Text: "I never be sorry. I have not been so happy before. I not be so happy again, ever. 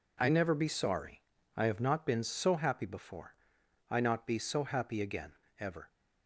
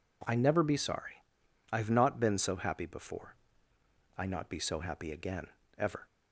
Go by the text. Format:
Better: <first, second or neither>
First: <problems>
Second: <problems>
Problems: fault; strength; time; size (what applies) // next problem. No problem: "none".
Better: neither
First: none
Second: none